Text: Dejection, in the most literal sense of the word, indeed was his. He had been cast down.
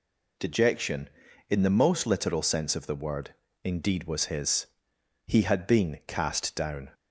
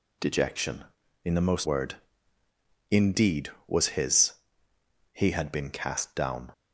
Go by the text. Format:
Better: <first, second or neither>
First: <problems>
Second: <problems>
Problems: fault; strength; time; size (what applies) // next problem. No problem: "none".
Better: first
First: none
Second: skips "literal sense of the"; at 1.6 s